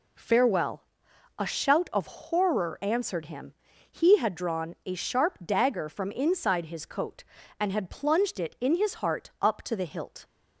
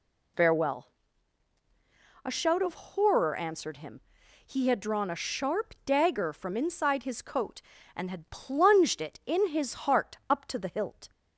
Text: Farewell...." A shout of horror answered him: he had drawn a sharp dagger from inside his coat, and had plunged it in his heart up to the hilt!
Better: neither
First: none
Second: none

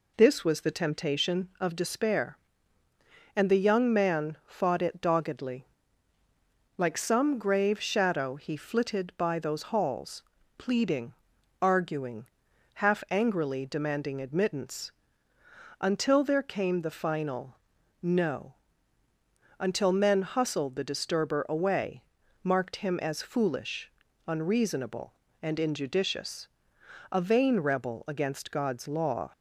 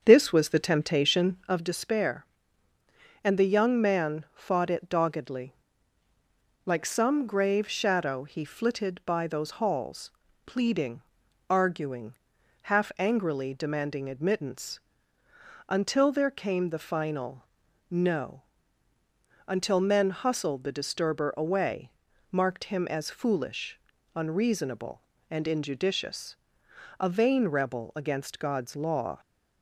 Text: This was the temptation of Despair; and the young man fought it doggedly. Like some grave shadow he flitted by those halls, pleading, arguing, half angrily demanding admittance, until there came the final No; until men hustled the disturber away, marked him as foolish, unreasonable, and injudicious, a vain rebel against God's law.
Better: first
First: pauses between "final" and "No"; at 17.5 s; 0.44 s long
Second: starts louder than the rest; until 1.7 s; 7 dB // pauses between "final" and "No"; at 17.4 s; 0.44 s long

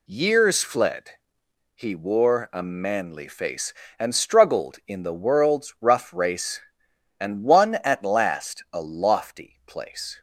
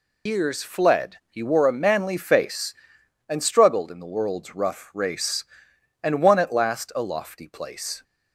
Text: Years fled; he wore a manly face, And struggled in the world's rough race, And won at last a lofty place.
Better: first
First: none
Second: loses the start of "Years"; at 0.2 s; 125 ms

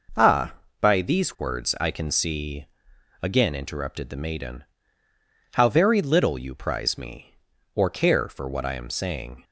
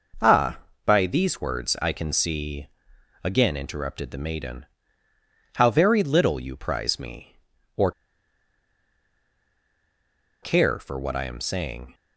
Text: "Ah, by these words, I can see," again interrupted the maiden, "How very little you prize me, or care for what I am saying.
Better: first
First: none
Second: pauses between "or" and "care"; strong; at 7.9 s; 2.5 s long

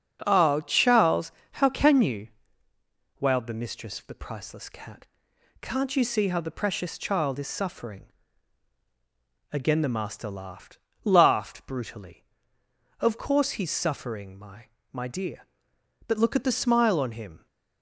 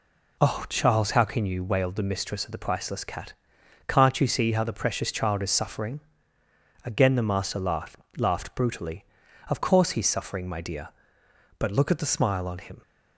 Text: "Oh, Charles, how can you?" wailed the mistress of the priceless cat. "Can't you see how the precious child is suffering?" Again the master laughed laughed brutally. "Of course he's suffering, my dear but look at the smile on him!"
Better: second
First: starts louder than the rest; until 1.2 s; 6.5 dB // pauses between "laughed" and "laughed"; slight; at 10.7 s; 0.28 s long // says "my" twice; at 14.9 s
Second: pauses between "laughed" and "laughed"; slight; at 7.9 s; 0.20 s long

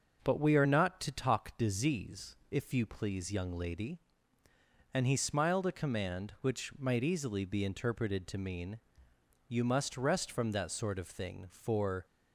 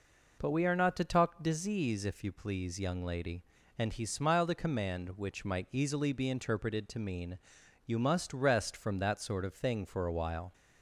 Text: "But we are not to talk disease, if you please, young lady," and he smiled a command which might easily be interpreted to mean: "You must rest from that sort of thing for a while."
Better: second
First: starts louder than the rest; until 1.2 s; 6 dB // stops before "a while"; at 12.0 s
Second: none

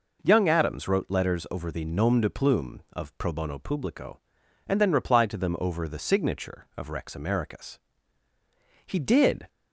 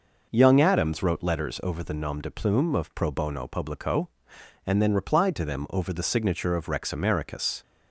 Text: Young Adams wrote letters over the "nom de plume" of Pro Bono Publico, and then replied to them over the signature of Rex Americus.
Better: second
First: goes on to say "He did"; noticeable; from 8.8 s on; 0.64 s long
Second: none

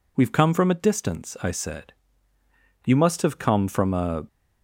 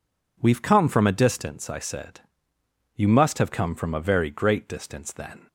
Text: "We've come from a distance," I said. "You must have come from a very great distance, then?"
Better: second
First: stops before "very great distance then"; at 4.2 s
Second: none

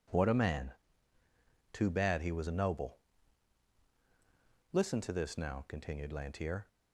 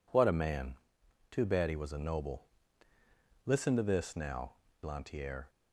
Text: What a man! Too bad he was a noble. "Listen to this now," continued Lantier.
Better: first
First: none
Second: skips "continued"; at 4.6 s

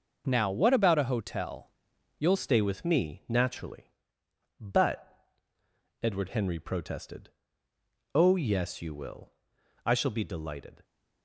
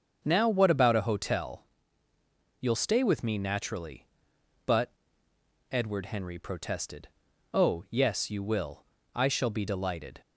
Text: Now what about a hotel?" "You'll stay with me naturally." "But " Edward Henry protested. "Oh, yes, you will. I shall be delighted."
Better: second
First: starts louder than the rest; until 1.2 s; 6.5 dB // changes voice at "stay"; from 2.3 s on; 8.5 s long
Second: starts louder than the rest; strong; until 1.2 s; 7.5 dB

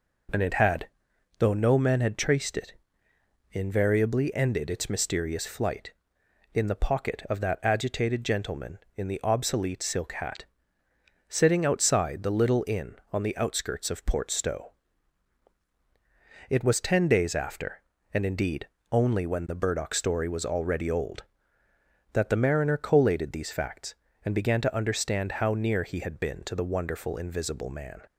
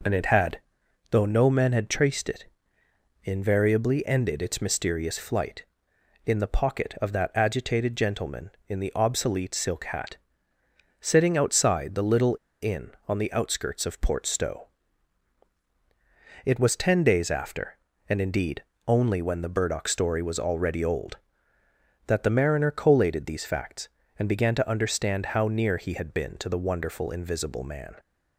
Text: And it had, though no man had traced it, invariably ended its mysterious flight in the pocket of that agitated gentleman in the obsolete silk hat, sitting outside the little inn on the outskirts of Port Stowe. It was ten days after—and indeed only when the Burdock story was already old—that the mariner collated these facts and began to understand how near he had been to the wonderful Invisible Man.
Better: first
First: pauses between "indeed" and "only"; slight; at 18.6 s; 0.26 s long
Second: pauses between "little" and "inn"; slight; at 12.3 s; 0.26 s long // pauses between "indeed" and "only"; slight; at 18.6 s; 0.26 s long

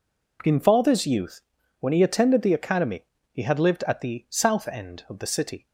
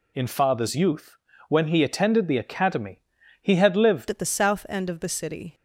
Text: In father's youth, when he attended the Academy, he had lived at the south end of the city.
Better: first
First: none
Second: changes voice at "at"; from 4.1 s on; 1.4 s long

